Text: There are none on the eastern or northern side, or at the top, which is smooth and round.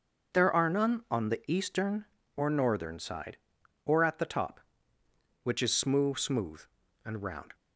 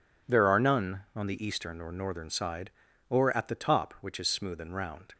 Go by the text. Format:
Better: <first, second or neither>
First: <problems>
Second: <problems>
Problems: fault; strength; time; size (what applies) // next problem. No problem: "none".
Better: second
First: says "smooth" twice; at 6.1 s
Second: none